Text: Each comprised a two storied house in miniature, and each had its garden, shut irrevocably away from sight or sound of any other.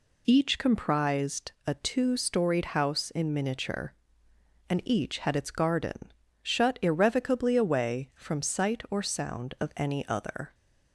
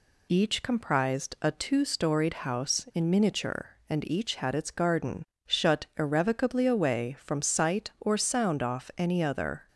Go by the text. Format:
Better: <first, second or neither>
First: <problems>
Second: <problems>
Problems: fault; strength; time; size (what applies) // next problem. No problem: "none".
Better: first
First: none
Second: says "off" for "of"; at 8.6 s